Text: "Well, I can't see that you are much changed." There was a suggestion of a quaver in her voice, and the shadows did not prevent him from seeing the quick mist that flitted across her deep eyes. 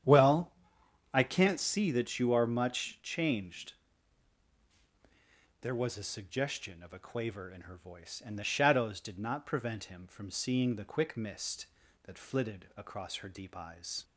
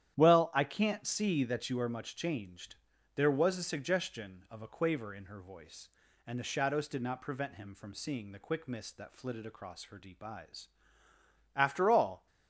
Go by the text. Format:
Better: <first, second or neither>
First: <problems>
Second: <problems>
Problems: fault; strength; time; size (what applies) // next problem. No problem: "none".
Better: first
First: starts louder than the rest; strong; until 1.6 s; 9.5 dB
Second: starts louder than the rest; strong; until 1.1 s; 11 dB // goes on to say "After all"; noticeable; from 11.5 s on; 0.70 s long